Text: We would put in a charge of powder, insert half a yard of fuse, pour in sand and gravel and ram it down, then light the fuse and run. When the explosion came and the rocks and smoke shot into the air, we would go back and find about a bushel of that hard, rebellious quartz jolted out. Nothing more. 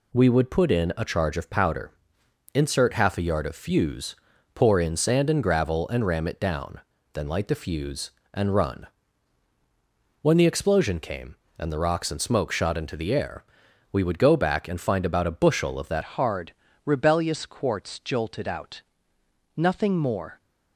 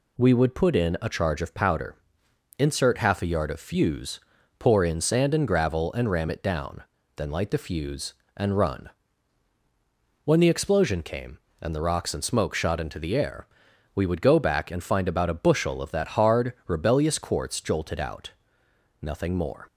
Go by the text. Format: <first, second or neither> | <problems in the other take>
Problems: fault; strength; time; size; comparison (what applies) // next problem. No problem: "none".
second | changes voice at "hard"; from 16.0 s on; 4.4 s long